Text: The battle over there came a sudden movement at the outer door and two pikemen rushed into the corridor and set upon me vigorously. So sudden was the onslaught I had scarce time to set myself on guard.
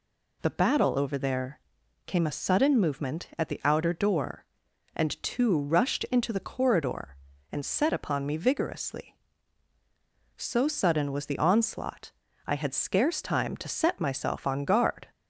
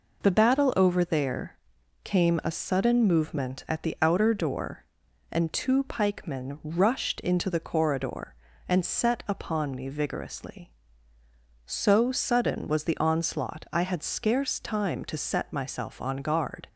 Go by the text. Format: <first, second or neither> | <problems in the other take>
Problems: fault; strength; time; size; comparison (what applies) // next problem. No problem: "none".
second | pauses between "there" and "came"; noticeable; at 1.5 s; 0.46 s long; noticeable in the second // skips "pikemen"; at 5.5 s // pauses between "onslaught" and "I"; slight; at 12.1 s; 0.36 s long